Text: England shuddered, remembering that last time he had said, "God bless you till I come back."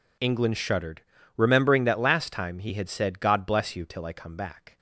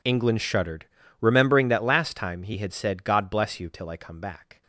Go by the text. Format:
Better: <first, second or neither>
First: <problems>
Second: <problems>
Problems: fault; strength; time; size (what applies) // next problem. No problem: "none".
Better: first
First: none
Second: gets quieter; strong; throughout; 22 dB